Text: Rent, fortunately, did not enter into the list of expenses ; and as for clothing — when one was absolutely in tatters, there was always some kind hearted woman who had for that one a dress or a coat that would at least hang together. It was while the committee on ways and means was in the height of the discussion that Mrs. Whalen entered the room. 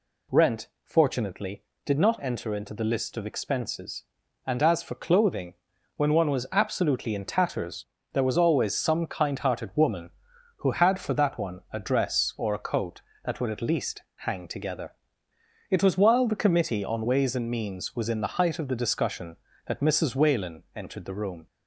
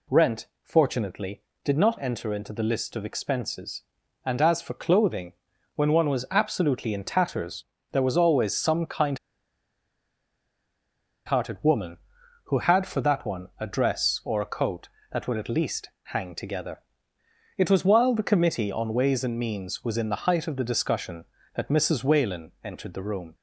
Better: first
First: none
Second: pauses between "kind" and "hearted"; strong; at 9.1 s; 2.0 s long

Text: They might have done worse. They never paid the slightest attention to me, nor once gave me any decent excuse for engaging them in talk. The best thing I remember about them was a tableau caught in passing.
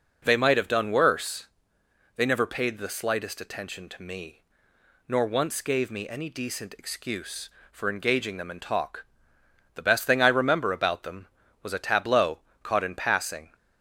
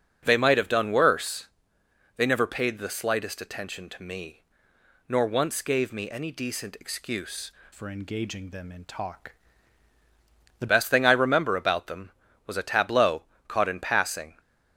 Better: first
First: pauses between "tableau" and "caught"; slight; at 12.3 s; 0.24 s long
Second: starts louder than the rest; strong; until 1.2 s; 7.5 dB // changes voice from "for" to "The"; from 7.7 to 10.6 s; 2.9 s long // pauses between "tableau" and "caught"; slight; at 13.2 s; 0.24 s long

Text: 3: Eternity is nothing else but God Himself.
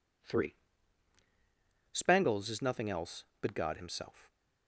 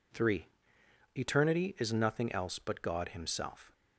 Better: second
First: says "Spangles" for "Eternity"; at 1.9 s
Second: none

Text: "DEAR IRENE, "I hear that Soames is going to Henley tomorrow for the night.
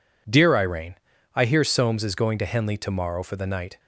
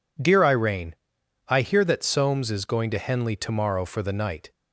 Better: second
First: skips "that"; at 1.6 s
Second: none

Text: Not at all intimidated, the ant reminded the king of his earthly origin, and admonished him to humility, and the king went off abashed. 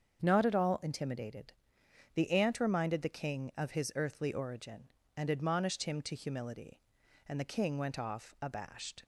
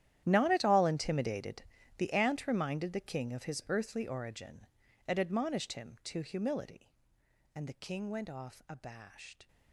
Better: first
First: starts louder than the rest; until 1.2 s; 7 dB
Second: gets quieter; strong; throughout; 19 dB // starts louder than the rest; strong; until 1.2 s; 11.5 dB

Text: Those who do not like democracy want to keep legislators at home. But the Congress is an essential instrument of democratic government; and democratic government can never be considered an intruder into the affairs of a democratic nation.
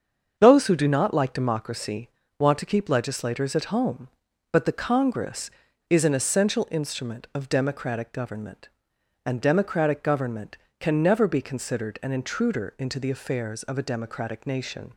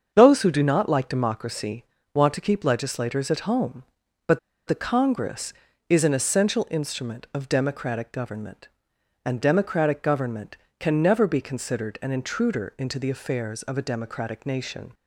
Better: first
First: starts louder than the rest; until 1.3 s; 7 dB // pauses between "democracy" and "want"; slight; at 2.0 s; 0.30 s long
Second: starts louder than the rest; until 1.1 s; 7 dB // pauses between "democracy" and "want"; slight; at 1.8 s; 0.30 s long // pauses between "But" and "the"; slight; at 4.3 s; 0.28 s long

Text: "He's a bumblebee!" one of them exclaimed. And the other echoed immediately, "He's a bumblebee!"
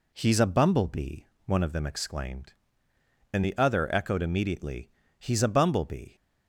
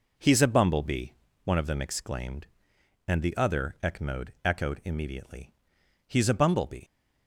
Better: first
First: none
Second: says "echoed" twice; at 4.4 s

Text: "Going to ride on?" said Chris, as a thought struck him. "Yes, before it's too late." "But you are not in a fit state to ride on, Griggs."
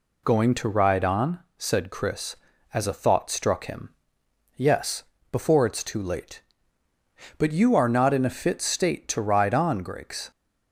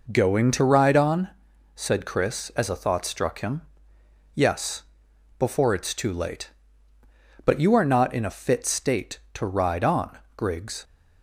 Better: first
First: none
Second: starts louder than the rest; noticeable; until 1.2 s; 5 dB

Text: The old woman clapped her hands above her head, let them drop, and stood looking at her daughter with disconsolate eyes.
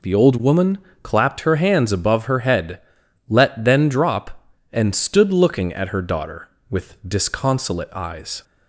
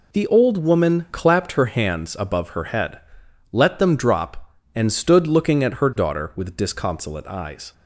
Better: second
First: pauses between "woman" and "clapped"; slight; at 0.7 s; 0.26 s long // says "then" for "them"; at 3.6 s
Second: none

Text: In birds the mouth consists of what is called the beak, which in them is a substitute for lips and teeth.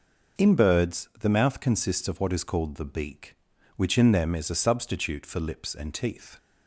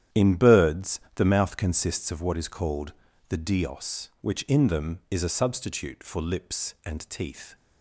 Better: first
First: none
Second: starts louder than the rest; strong; until 1.2 s; 10.5 dB // pauses between "birds" and "the"; slight; at 0.9 s; 0.16 s long // pauses between "called" and "the"; slight; at 2.9 s; 0.36 s long // says "dios" for "beak"; at 3.3 s

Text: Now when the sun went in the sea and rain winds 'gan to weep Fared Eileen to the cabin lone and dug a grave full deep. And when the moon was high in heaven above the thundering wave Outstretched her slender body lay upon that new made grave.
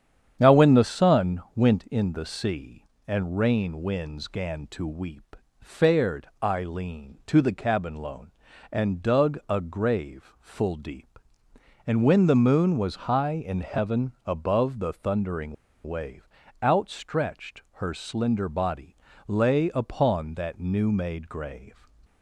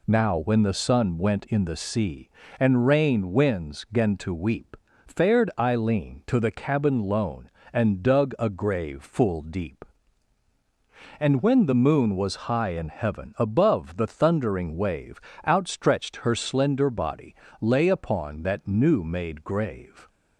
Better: second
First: starts louder than the rest; strong; until 1.4 s; 8.5 dB // pauses between "weep" and "Fared"; slight; at 5.3 s; 0.24 s long // pauses between "heaven" and "above"; slight; at 14.1 s; 0.16 s long // pauses between "thundering" and "wave"; slight; at 15.5 s; 0.30 s long // pauses between "wave" and "Outstretched"; at 16.2 s; 0.38 s long // pauses between "body" and "lay"; slight; at 18.9 s; 0.32 s long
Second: pauses between "weep" and "Fared"; slight; at 4.7 s; 0.30 s long // pauses between "wave" and "Outstretched"; slight; at 15.2 s; 0.26 s long // pauses between "body" and "lay"; slight; at 17.3 s; 0.24 s long

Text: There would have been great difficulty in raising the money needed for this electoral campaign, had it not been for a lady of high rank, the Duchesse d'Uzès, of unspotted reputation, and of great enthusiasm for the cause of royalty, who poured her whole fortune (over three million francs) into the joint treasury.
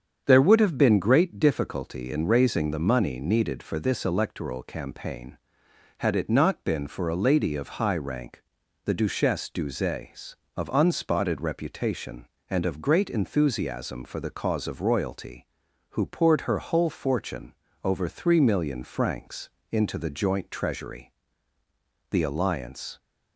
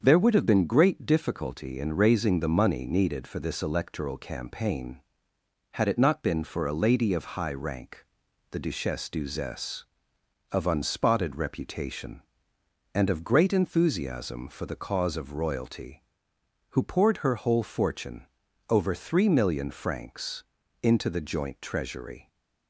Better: second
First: starts louder than the rest; strong; until 1.2 s; 7.5 dB // goes on to say "The alliance"; noticeable; from 22.1 s on; 0.88 s long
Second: starts louder than the rest; until 1.0 s; 7 dB

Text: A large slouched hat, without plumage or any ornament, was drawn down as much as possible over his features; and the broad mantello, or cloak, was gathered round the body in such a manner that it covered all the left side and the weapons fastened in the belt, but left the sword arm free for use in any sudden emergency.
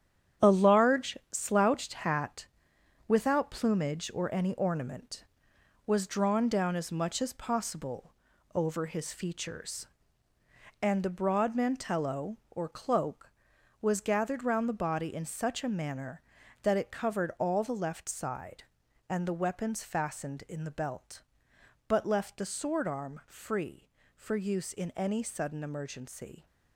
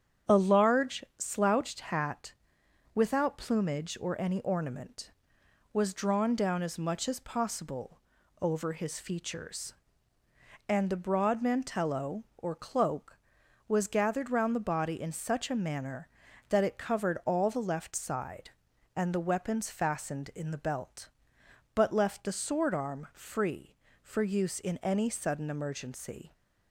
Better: second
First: gets quieter; strong; throughout; 8.5 dB // starts louder than the rest; strong; until 1.5 s; 9.5 dB // pauses between "possible" and "over"; at 8.1 s; 0.42 s long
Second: starts louder than the rest; strong; until 1.4 s; 8.5 dB // pauses between "possible" and "over"; at 8.0 s; 0.42 s long

